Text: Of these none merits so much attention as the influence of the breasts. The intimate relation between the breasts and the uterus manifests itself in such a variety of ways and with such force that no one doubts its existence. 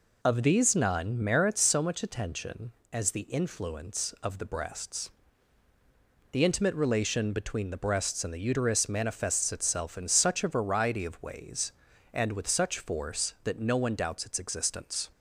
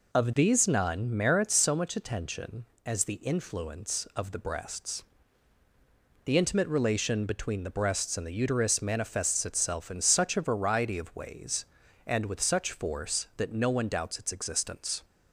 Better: neither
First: none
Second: none

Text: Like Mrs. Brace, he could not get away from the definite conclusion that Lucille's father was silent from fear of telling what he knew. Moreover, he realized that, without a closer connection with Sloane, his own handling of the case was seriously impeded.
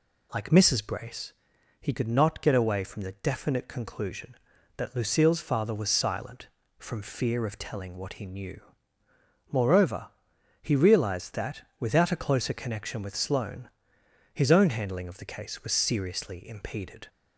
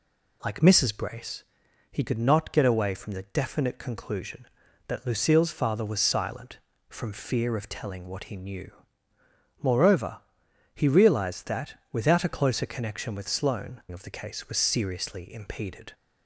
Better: first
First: none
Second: skips "his own handling"; at 13.8 s

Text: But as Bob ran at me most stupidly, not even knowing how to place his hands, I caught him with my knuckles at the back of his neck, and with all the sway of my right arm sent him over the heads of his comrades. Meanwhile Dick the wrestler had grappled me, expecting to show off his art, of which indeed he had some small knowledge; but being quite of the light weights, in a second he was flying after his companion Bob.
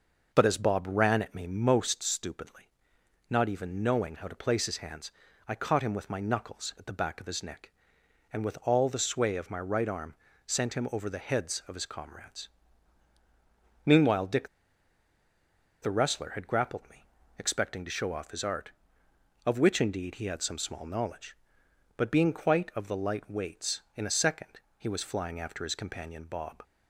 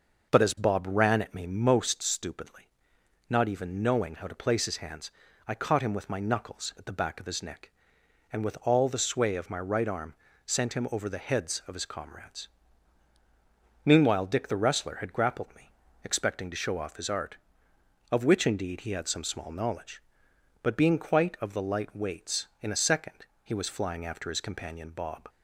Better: second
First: starts louder than the rest; noticeable; until 1.3 s; 6 dB // pauses between "arm" and "sent"; slight; at 10.1 s; 0.32 s long // pauses between "Dick" and "the"; strong; at 14.4 s; 1.3 s long // pauses between "second" and "he"; slight; at 24.6 s; 0.18 s long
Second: starts louder than the rest; noticeable; until 1.3 s; 6 dB // pauses between "arm" and "sent"; slight; at 10.1 s; 0.32 s long // pauses between "second" and "he"; slight; at 23.2 s; 0.18 s long

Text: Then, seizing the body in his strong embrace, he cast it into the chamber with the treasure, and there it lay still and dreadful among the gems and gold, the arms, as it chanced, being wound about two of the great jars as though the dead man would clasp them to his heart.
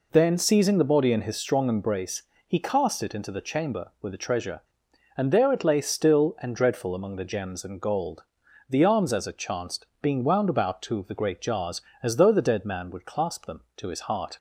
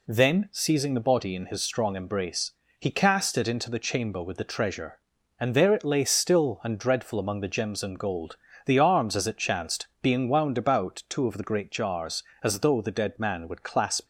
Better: first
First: none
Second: stops before "them to his heart"; at 14.0 s

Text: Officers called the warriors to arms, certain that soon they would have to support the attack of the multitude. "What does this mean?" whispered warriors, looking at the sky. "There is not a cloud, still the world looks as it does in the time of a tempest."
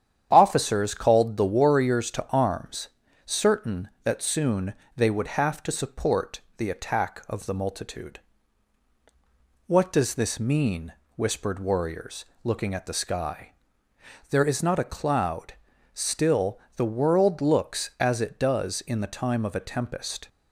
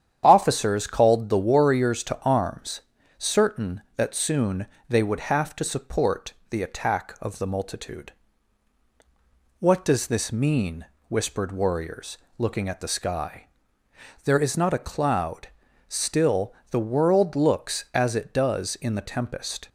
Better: first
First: starts louder than the rest; strong; until 1.3 s; 9 dB // pauses between "soon" and "they"; slight; at 4.7 s; 0.24 s long // pauses between "support" and "the"; slight; at 6.3 s; 0.16 s long // pauses between "still" and "the"; slight; at 16.5 s; 0.16 s long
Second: starts louder than the rest; strong; until 1.2 s; 9 dB // pauses between "soon" and "they"; slight; at 4.6 s; 0.24 s long // pauses between "support" and "the"; slight; at 6.3 s; 0.16 s long // pauses between "still" and "the"; slight; at 16.5 s; 0.16 s long // skips "time of a"; at 19.0 s

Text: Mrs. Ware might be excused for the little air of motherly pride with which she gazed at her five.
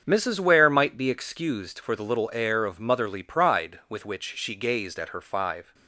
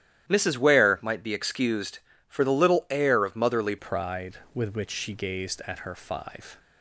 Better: first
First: starts louder than the rest; strong; until 1.0 s; 7.5 dB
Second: starts louder than the rest; strong; until 1.3 s; 11.5 dB // changes voice at "pride"; from 3.7 s on; 2.8 s long

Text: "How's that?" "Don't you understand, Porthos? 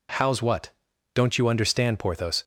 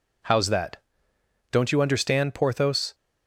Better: second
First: says "what" for "that"; at 0.4 s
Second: none

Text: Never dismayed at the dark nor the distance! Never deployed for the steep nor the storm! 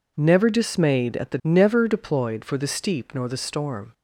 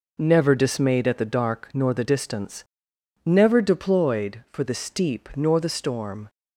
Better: second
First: skips "dark nor the distance"; at 1.4 s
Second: none

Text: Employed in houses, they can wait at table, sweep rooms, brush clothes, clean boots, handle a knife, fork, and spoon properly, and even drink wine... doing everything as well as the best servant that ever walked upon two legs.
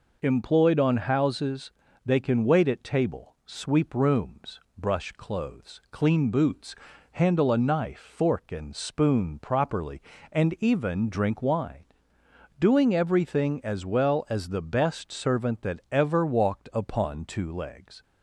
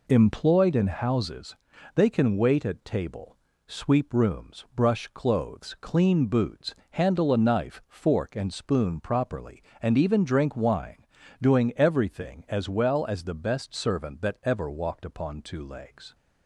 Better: second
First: says "on" for "in"; at 0.7 s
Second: none

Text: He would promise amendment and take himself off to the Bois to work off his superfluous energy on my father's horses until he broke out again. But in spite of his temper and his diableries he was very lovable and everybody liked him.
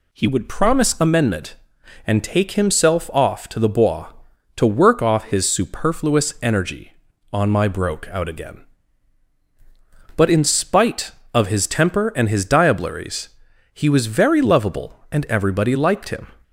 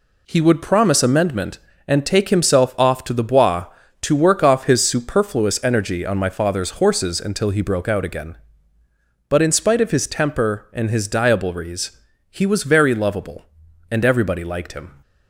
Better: second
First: skips "father's horses until he"; at 7.6 s // pauses between "diableries" and "he"; noticeable; at 13.2 s; 0.46 s long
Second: pauses between "diableries" and "he"; slight; at 11.9 s; 0.34 s long

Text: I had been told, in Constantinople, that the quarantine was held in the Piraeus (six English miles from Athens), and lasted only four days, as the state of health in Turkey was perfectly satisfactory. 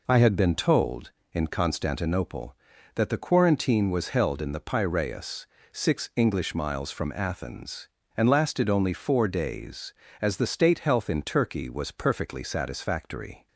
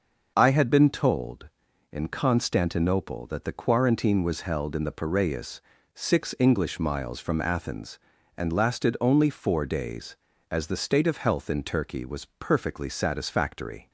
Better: second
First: skips "of"; at 10.7 s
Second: none

